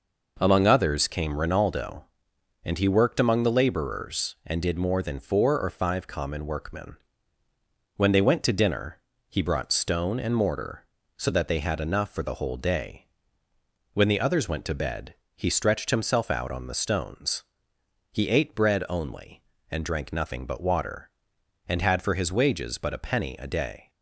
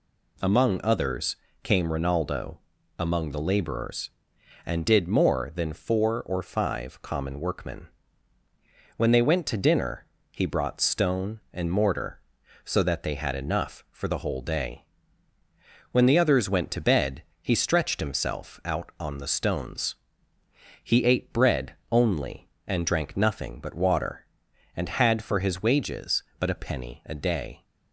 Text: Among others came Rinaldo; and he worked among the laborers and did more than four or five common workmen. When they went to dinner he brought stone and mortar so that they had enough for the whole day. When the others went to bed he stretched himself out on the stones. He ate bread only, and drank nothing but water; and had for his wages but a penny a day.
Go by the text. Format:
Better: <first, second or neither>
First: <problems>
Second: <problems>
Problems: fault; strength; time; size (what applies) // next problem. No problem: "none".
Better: first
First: pauses between "dinner" and "he"; slight; at 8.9 s; 0.30 s long // pauses between "bed" and "he"; slight; at 15.1 s; 0.18 s long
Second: pauses between "others" and "came"; slight; at 1.3 s; 0.28 s long // skips "and he worked"; at 2.7 s // pauses between "dinner" and "he"; slight; at 10.0 s; 0.26 s long // pauses between "bed" and "he"; slight; at 17.2 s; 0.18 s long // pauses between "bread" and "only"; slight; at 21.7 s; 0.16 s long